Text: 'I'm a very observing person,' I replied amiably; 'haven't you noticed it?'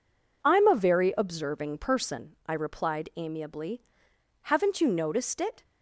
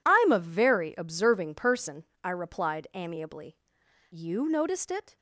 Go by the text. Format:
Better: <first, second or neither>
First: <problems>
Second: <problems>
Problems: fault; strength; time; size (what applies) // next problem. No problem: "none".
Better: first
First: none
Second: skips "haven't"; at 3.8 s